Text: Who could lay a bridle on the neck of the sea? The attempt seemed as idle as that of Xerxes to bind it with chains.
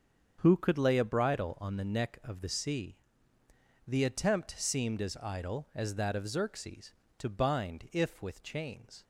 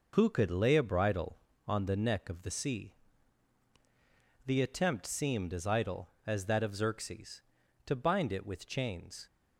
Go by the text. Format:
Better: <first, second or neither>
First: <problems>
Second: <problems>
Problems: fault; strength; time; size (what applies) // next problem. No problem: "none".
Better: second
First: starts louder than the rest; strong; until 1.4 s; 7.5 dB // says "if" for "it"; at 7.9 s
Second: none